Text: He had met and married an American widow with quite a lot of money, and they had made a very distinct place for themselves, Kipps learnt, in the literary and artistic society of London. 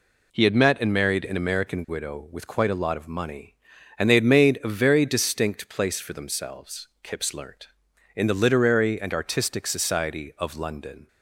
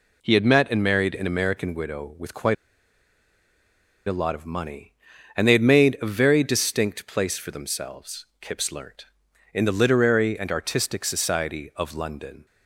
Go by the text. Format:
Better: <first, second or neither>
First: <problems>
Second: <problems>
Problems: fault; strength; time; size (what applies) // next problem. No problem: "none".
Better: first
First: none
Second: pauses between "quite" and "a"; strong; at 2.5 s; 1.5 s long